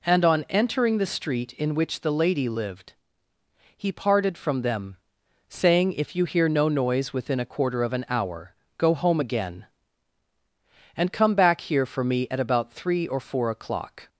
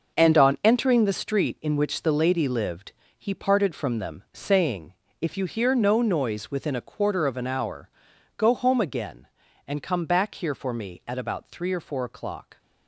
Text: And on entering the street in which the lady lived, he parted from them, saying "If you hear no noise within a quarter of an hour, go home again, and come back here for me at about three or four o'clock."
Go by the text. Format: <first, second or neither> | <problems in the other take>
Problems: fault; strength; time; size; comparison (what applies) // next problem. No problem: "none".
first | gets quieter; strong; throughout; 10.5 dB // pauses between "saying" and "If"; slight; at 4.9 s; 0.30 s long